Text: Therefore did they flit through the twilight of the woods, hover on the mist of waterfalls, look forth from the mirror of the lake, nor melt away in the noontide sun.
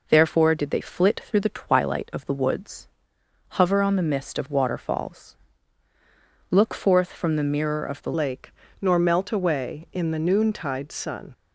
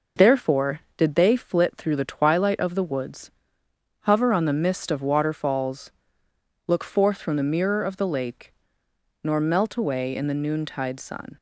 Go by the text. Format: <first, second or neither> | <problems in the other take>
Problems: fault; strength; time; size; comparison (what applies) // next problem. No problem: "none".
second | changes voice at "lake"; from 8.1 s on; 3.2 s long